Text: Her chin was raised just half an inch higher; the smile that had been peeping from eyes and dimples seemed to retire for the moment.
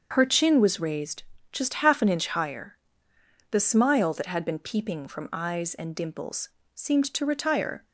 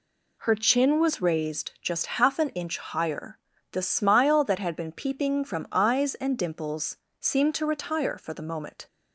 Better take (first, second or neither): second